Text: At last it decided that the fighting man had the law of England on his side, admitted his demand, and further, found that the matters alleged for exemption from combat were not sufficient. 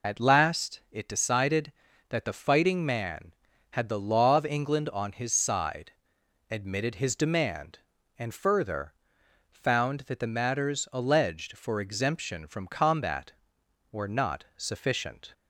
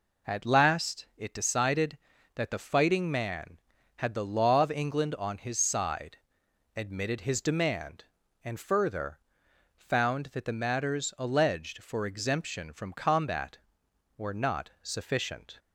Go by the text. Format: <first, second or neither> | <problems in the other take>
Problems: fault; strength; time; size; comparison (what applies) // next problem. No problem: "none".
second | loses the start of "At"; at 0.0 s; 35 ms